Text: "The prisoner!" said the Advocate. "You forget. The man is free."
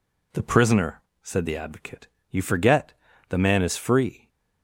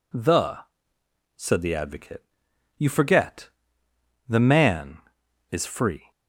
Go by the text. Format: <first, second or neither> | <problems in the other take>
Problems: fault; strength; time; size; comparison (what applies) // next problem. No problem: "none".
first | skips "prisoner"; at 0.9 s